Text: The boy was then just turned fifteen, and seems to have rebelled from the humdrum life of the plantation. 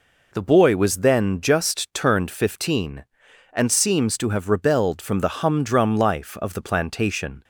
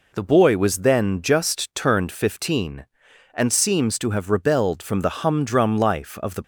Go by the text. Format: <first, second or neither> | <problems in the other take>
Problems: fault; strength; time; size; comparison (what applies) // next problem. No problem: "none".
first | stops before "plantation"; at 6.4 s